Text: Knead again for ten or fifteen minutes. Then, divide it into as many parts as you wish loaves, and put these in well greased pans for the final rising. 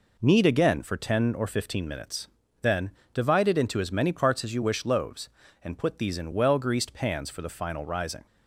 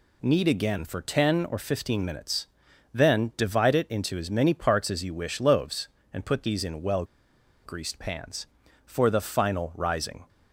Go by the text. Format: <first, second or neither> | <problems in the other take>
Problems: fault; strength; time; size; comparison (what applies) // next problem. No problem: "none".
first | pauses between "well" and "greased"; noticeable; at 7.0 s; 0.59 s long